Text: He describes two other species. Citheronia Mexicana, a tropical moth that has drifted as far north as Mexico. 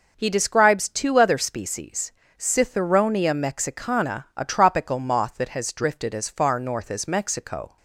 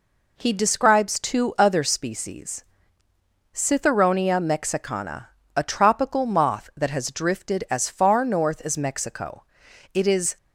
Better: first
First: none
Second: goes on to say "It is"; slight; from 9.9 s on; 0.44 s long

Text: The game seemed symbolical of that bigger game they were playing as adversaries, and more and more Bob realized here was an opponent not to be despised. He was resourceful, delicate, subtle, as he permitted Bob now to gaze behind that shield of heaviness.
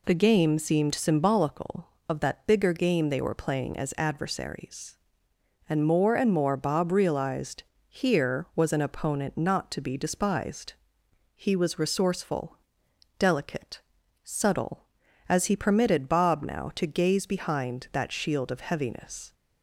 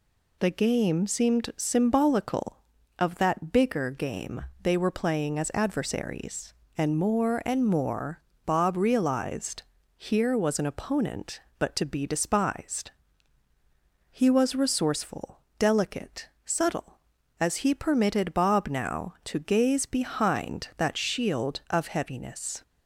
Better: first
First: pauses between "realized" and "here"; slight; at 7.6 s; 0.26 s long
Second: pauses between "game" and "they"; slight; at 4.4 s; 0.18 s long // pauses between "more" and "Bob"; slight; at 8.2 s; 0.24 s long // pauses between "realized" and "here"; slight; at 9.6 s; 0.34 s long // says "but" for "not"; at 11.5 s

